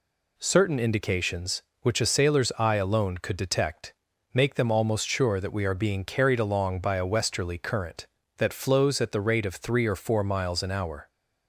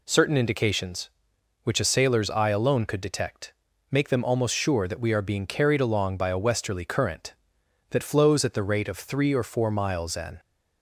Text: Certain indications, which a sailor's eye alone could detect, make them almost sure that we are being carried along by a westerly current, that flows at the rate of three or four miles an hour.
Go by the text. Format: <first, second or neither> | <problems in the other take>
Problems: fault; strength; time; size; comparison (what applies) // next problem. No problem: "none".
first | stops before "hour"; at 10.3 s